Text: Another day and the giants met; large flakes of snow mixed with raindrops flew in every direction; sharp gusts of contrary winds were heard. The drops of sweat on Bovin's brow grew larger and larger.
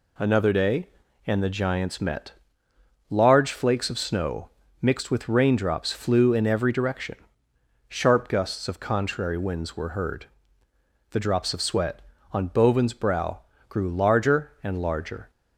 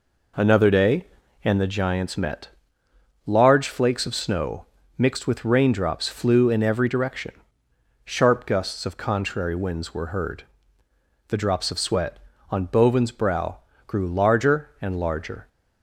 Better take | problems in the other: first | starts louder than the rest; noticeable; until 1.7 s; 4 dB // pauses between "snow" and "mixed"; slight; at 4.6 s; 0.32 s long; slight in the first // pauses between "brow" and "grew"; slight; at 13.5 s; 0.28 s long; slight in the first

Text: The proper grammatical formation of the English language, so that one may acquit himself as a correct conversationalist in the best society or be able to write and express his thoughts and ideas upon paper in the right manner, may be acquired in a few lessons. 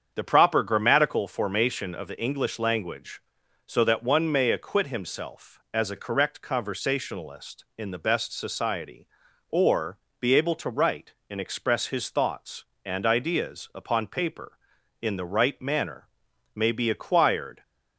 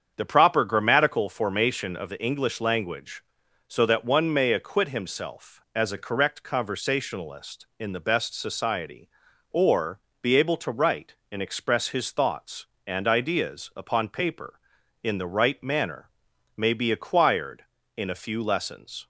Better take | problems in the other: second | starts louder than the rest; strong; until 1.1 s; 7.5 dB; strong in the second // pauses between "or" and "be"; slight; at 9.9 s; 0.24 s long; slight in the second // stops before "in a few lessons"; at 17.6 s

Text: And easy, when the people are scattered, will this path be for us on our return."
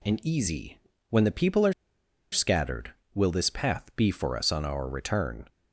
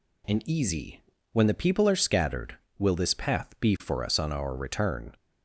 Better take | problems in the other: second | pauses between "are" and "scattered"; noticeable; at 1.7 s; 0.59 s long

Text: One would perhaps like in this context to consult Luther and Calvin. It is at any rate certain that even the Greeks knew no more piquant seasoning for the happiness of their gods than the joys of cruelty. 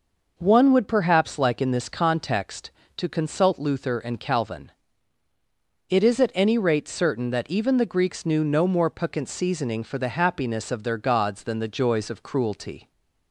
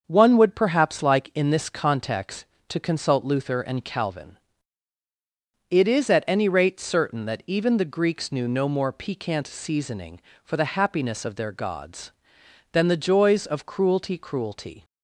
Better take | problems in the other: first | starts louder than the rest; until 1.0 s; 6.5 dB // says "cruelty" twice; at 14.1 s

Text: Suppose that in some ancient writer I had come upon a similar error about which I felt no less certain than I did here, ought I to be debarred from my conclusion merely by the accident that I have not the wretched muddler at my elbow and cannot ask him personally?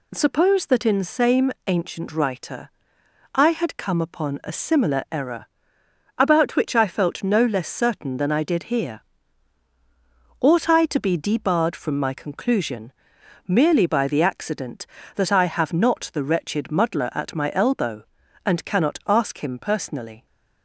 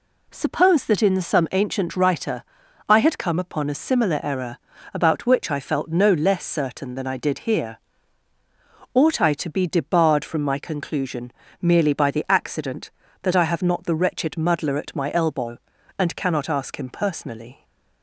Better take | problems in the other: second | says "same" for "some"; at 1.0 s // pauses between "writer" and "I"; noticeable; at 2.7 s; 0.64 s long; also in the second // pauses between "error" and "about"; noticeable; at 5.4 s; 0.72 s long; slight in the second // pauses between "conclusion" and "merely"; noticeable; at 12.9 s; 0.56 s long; slight in the second

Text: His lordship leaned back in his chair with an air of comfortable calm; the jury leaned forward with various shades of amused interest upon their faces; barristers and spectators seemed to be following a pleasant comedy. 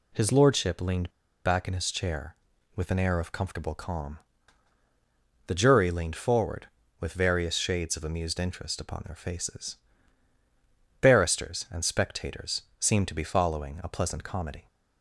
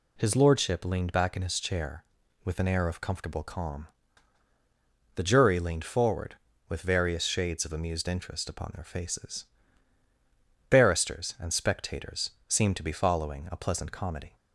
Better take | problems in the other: second | pauses between "leaned" and "back"; slight; at 1.0 s; 0.35 s long // pauses between "spectators" and "seemed"; slight; at 12.6 s; 0.18 s long; slight in the second

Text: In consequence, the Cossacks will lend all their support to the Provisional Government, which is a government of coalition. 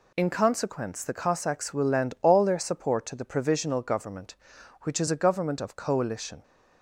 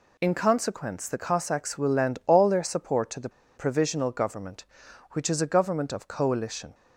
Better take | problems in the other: first | pauses between "the" and "Provisional"; slight; at 3.2 s; 0.27 s long

